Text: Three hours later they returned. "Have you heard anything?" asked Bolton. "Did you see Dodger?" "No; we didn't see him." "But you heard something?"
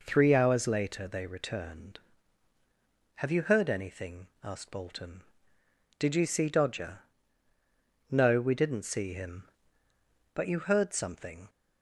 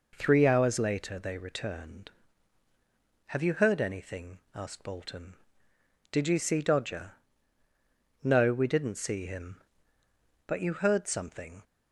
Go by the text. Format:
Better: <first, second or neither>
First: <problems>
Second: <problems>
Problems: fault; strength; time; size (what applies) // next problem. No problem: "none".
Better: neither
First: none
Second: none